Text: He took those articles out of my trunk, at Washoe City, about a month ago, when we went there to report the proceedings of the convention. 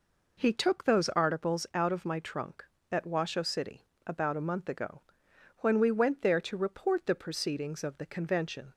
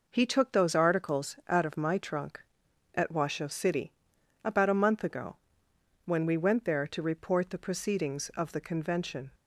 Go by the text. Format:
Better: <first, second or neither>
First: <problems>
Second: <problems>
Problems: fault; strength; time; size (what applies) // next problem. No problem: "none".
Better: neither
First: none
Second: none